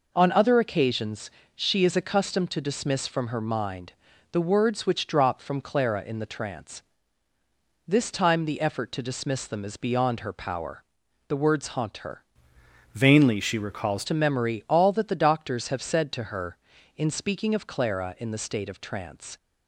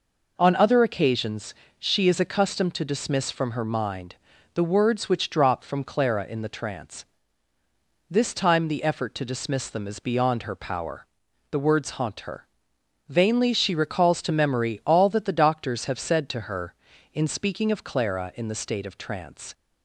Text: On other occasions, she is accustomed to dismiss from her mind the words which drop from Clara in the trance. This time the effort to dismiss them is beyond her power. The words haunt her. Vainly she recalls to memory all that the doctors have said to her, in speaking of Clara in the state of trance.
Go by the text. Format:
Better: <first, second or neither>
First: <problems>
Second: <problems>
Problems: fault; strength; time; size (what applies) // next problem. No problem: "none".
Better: second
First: pauses between "mind" and "the"; at 3.9 s; 0.38 s long // changes voice from "Vainly" to "recalls"; from 12.9 to 14.0 s; 1.1 s long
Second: pauses between "mind" and "the"; at 4.1 s; 0.38 s long